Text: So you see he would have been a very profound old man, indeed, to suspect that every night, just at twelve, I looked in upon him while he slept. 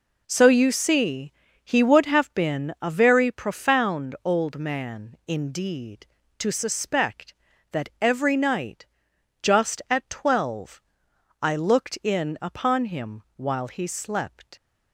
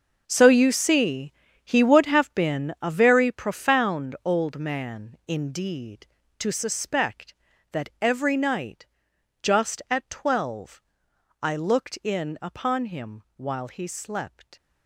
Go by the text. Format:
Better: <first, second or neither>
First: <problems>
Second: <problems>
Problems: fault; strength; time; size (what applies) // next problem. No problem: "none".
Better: first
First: pauses between "see" and "he"; slight; at 1.3 s; 0.30 s long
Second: gets quieter; strong; throughout; 12 dB // pauses between "see" and "he"; slight; at 1.3 s; 0.30 s long